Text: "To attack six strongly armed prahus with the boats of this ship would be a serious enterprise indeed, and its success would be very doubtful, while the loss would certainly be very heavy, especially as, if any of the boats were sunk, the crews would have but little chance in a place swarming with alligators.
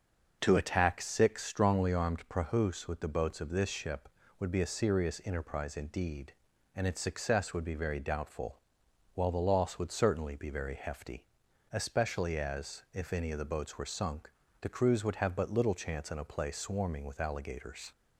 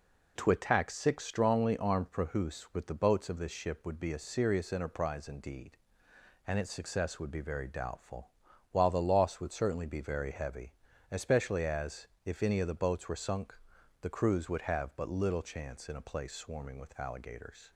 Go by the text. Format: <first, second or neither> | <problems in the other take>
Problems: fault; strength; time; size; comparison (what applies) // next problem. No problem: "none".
second | starts louder than the rest; until 1.4 s; 6.5 dB // says "hefty" for "heavy"; at 10.7 s